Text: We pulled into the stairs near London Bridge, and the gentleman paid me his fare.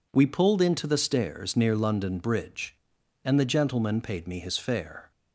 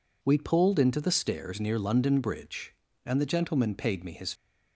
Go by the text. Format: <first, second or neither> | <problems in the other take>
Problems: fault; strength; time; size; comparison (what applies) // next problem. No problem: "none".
first | stops before "fare"; at 4.3 s